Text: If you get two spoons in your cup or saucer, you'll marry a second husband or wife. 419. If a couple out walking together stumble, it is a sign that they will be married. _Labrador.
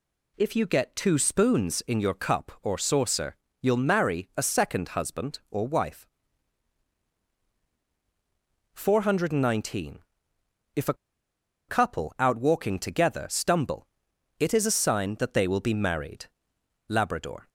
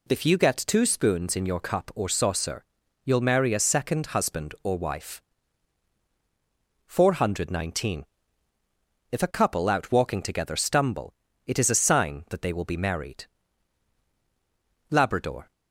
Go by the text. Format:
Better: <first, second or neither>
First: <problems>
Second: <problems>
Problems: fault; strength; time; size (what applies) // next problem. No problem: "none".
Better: second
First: pauses between "a" and "couple"; noticeable; at 10.9 s; 0.74 s long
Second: none